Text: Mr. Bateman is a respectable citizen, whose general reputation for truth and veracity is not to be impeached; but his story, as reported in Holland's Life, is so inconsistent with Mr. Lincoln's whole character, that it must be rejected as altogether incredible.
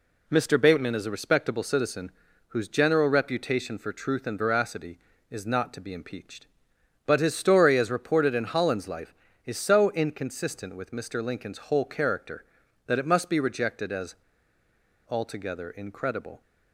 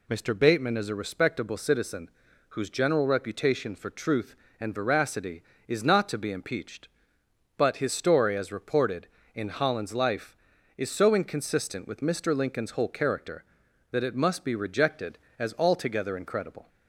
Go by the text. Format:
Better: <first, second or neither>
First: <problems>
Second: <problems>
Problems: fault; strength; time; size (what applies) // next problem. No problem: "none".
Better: second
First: pauses between "as" and "altogether"; noticeable; at 14.1 s; 0.90 s long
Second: none